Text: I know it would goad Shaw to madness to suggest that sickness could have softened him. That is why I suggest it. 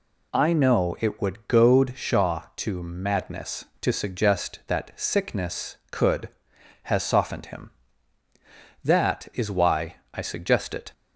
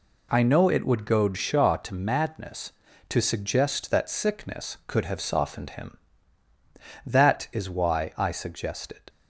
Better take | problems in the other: second | says "has" for "have"; at 6.8 s // pauses between "why" and "I"; slight; at 9.9 s; 0.16 s long

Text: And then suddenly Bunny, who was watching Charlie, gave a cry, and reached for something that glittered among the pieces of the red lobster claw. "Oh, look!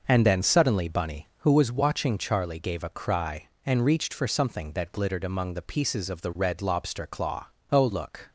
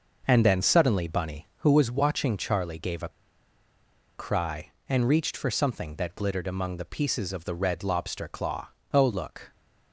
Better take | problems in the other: first | pauses between "a" and "cry"; at 3.0 s; 1.0 s long

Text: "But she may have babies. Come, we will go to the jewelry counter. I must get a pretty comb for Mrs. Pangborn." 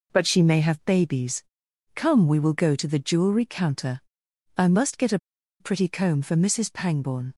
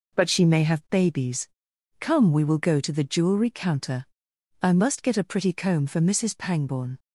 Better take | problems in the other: second | pauses between "a" and "pretty"; at 5.1 s; 0.42 s long

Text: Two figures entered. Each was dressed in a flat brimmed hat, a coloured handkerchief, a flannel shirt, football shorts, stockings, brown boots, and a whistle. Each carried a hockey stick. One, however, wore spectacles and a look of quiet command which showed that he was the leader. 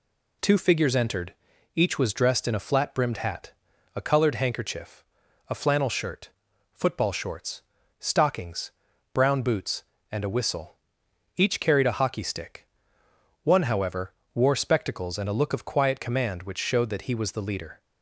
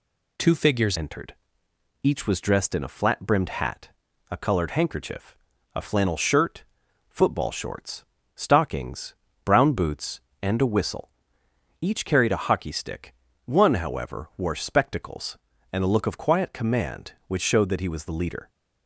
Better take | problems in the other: first | changes voice at "entered"; from 0.9 s on; 17.5 s long

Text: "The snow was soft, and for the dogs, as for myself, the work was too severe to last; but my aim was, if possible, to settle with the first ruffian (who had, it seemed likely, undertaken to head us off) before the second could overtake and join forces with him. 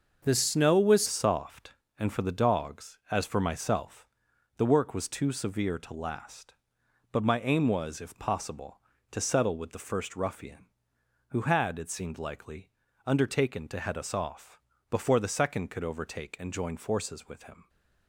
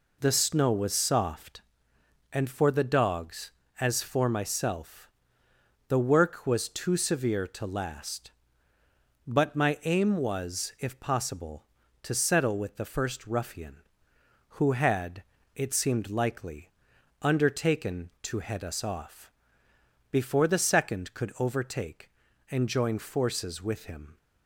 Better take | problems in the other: second | starts louder than the rest; until 1.2 s; 6.5 dB // changes voice at "soft"; from 1.0 s on; 16.6 s long

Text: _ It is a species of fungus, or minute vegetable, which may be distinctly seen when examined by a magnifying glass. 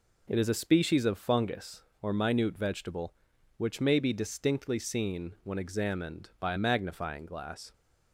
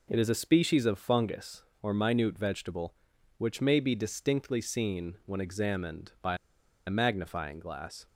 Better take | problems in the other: first | pauses between "by" and "a"; noticeable; at 6.3 s; 0.51 s long

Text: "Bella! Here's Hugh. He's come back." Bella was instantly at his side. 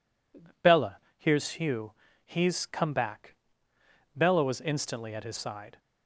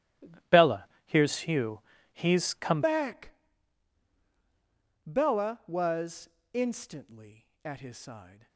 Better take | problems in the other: first | starts louder than the rest; strong; until 1.6 s; 13.5 dB // changes voice at "back"; from 2.8 s on; 5.6 s long // pauses between "was" and "instantly"; slight; at 6.2 s; 0.24 s long

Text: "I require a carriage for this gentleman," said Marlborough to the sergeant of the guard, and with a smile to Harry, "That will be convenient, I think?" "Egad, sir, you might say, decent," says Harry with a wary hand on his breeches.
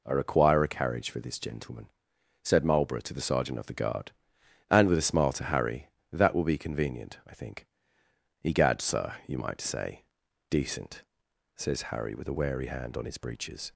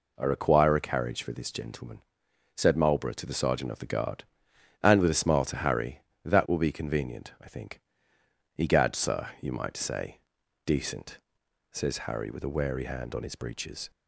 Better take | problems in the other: neither | none

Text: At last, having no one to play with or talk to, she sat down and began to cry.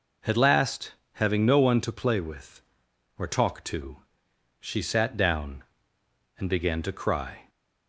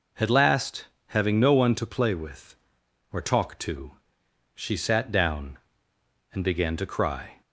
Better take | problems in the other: neither | none

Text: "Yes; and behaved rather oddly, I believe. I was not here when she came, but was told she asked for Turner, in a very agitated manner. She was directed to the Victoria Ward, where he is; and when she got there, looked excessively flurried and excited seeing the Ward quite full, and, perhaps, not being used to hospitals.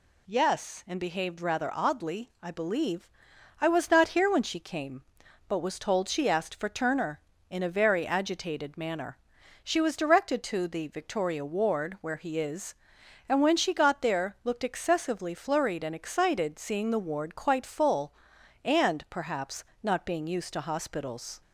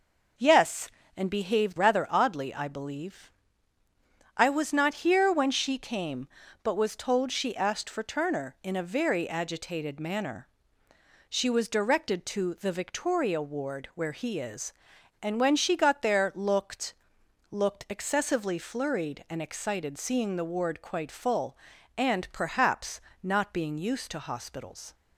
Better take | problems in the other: first | says "looked" twice; at 17.4 s

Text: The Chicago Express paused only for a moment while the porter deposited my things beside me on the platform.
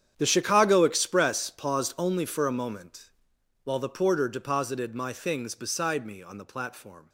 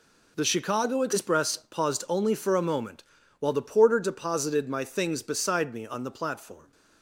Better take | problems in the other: second | gets quieter; strong; throughout; 15.5 dB // pauses between "moment" and "while"; noticeable; at 3.0 s; 0.56 s long; slight in the second

